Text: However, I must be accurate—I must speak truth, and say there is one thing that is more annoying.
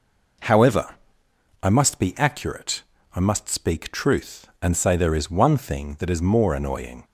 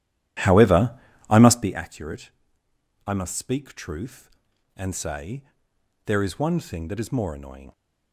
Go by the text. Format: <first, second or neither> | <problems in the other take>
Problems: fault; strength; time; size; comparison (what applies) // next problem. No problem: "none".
first | starts louder than the rest; strong; until 1.8 s; 12 dB // pauses between "say" and "there"; noticeable; at 5.4 s; 0.64 s long